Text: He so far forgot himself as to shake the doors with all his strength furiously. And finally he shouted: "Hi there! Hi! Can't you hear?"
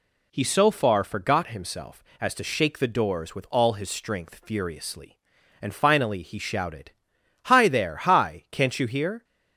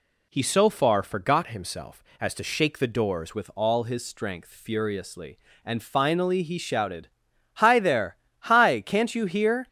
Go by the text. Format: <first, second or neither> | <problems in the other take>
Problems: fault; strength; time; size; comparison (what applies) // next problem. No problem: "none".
first | changes voice at "with"; from 3.3 s on; 6.3 s long